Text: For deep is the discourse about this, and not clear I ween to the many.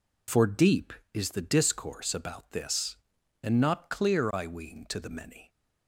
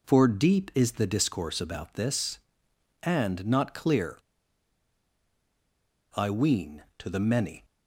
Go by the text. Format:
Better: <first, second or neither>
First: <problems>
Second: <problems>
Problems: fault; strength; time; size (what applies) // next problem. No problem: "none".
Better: first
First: none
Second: pauses between "clear" and "I"; strong; at 4.1 s; 1.9 s long